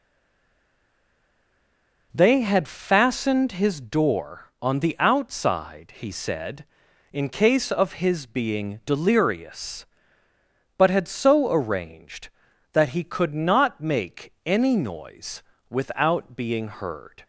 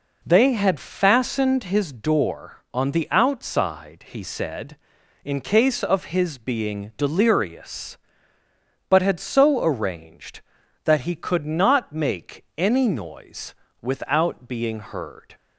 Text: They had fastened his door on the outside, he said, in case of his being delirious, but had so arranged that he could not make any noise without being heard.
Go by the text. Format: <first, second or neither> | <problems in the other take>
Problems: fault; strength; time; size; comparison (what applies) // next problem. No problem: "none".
second | stays silent before the first word; until 2.1 s; 2.1 s long // pauses between "noise" and "without"; slight; at 15.4 s; 0.28 s long; slight in the second